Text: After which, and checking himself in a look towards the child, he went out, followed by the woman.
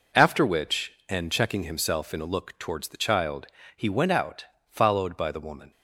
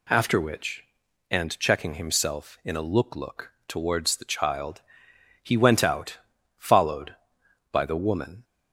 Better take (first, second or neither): first